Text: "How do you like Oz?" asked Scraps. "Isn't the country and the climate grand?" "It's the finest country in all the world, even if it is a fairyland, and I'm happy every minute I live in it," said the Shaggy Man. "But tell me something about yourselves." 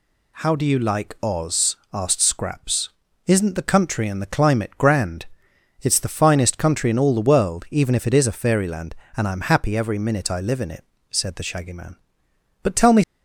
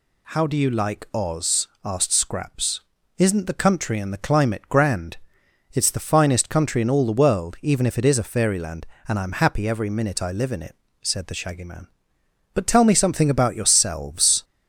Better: second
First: stops before "something about yourselves"; at 13.0 s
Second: none

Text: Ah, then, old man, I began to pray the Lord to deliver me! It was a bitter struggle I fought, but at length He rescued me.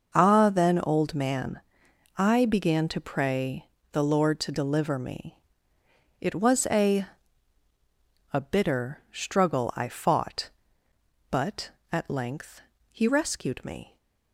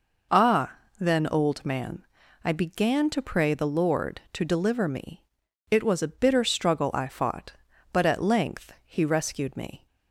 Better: second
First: starts louder than the rest; noticeable; until 1.1 s; 6 dB // pauses between "pray" and "the"; slight; at 3.6 s; 0.26 s long // says "a" twice; at 8.3 s // pauses between "length" and "He"; slight; at 12.6 s; 0.28 s long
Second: none

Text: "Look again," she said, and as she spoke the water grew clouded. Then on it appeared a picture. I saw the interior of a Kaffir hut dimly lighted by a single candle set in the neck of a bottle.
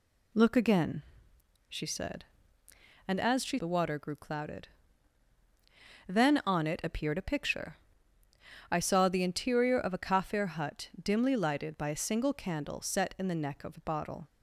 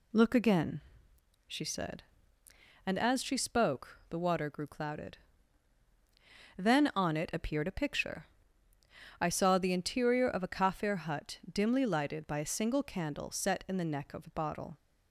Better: second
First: skips "spoke"; at 3.5 s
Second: none

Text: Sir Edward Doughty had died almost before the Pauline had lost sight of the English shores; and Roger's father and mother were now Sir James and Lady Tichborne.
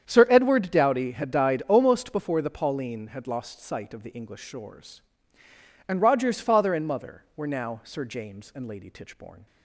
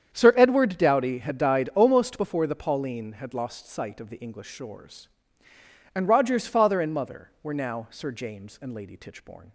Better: neither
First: starts louder than the rest; strong; until 1.0 s; 8.5 dB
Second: starts louder than the rest; strong; until 1.1 s; 8.5 dB

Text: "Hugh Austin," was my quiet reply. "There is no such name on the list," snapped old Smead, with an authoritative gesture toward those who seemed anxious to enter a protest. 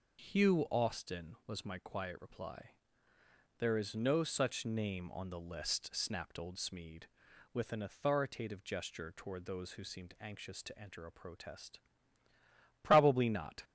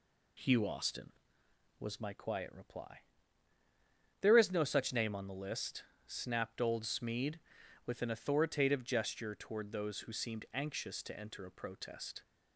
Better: second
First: goes on to say "Probably not"; noticeable; from 12.8 s on; 0.80 s long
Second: none

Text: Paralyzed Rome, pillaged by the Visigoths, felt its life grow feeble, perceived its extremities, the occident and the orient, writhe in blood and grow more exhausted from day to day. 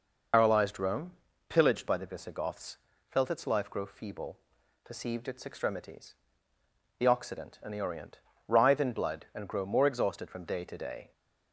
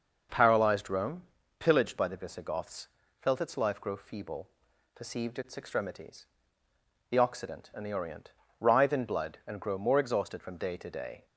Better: second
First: loses the start of "Paralyzed"; at 0.3 s; 140 ms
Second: none

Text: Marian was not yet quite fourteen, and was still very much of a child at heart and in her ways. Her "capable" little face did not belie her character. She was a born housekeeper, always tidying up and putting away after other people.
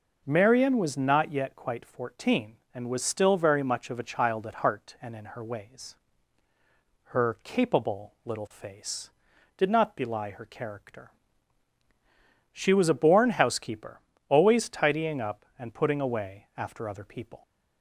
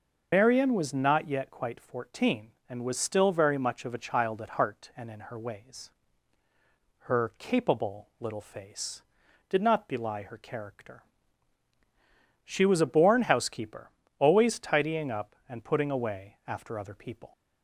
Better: first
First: none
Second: loses the start of "Marian"; at 0.3 s; 110 ms

